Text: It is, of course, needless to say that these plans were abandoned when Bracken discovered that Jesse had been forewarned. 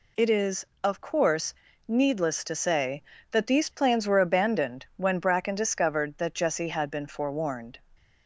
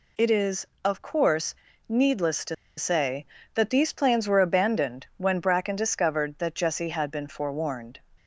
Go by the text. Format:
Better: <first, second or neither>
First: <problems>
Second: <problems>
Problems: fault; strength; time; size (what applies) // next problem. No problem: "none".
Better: first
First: none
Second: pauses between "to" and "say"; slight; at 2.5 s; 0.22 s long